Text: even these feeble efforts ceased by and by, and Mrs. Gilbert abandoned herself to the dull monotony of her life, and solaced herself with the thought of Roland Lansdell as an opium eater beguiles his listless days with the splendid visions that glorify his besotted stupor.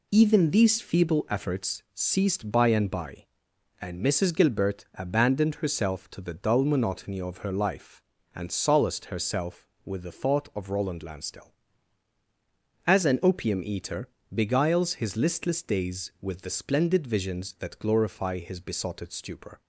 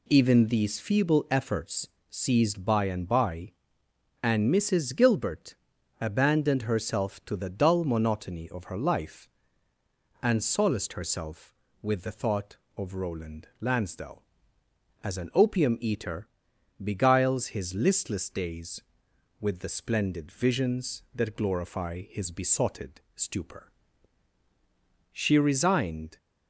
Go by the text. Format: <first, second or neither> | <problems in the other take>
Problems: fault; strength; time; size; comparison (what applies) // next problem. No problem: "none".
first | pauses between "efforts" and "ceased"; slight; at 1.8 s; 0.20 s long // pauses between "Gilbert" and "abandoned"; at 5.5 s; 0.44 s long // pauses between "eater" and "beguiles"; noticeable; at 16.2 s; 0.56 s long; slight in the first // pauses between "besotted" and "stupor"; slight; at 22.9 s; 0.16 s long // goes on to say "She resigned"; noticeable; from 25.1 s on; 1.0 s long